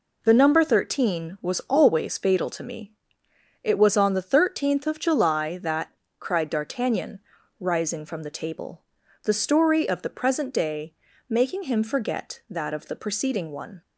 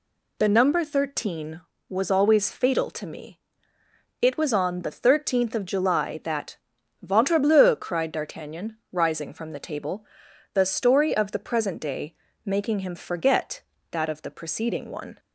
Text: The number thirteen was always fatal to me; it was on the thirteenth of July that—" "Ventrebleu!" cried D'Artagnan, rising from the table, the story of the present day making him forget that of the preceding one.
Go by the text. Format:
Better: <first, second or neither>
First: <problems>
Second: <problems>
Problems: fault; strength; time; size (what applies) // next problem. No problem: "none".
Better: second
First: skips "Ventrebleu"; at 6.0 s // pauses between "day" and "making"; slight; at 10.9 s; 0.34 s long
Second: pauses between "day" and "making"; slight; at 12.1 s; 0.32 s long